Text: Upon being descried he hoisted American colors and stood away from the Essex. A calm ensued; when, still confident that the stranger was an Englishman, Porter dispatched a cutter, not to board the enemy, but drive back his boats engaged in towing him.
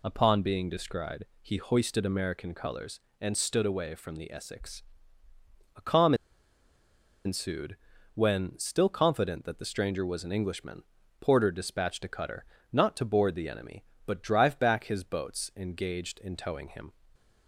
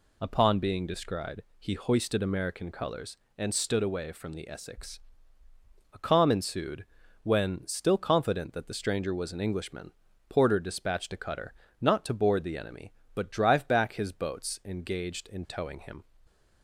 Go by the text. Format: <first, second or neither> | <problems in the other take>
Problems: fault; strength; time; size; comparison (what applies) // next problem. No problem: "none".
second | pauses between "descried" and "he"; slight; at 1.2 s; 0.18 s long; slight in the second // pauses between "calm" and "ensued"; at 6.1 s; 1.1 s long